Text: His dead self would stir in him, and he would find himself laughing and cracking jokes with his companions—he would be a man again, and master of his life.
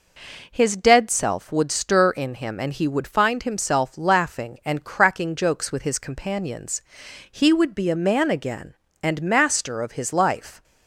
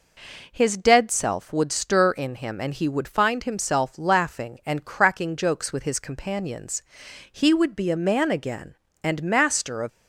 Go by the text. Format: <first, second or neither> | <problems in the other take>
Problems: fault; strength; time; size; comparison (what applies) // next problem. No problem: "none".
first | stops before "his life"; at 9.8 s